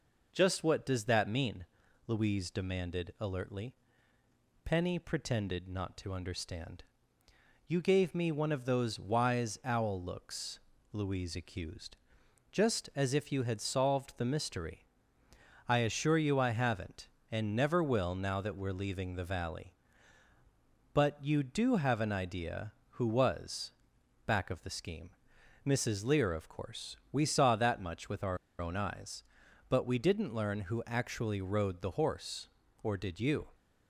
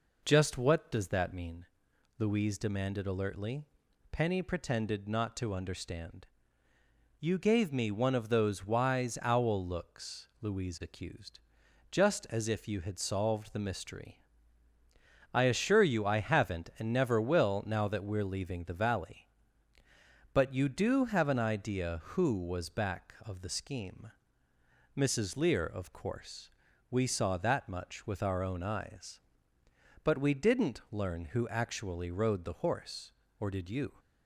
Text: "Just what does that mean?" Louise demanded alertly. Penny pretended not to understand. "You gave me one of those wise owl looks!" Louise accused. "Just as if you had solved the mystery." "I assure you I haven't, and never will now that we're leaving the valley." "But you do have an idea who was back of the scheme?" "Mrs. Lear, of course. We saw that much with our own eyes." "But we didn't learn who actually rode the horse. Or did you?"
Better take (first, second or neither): second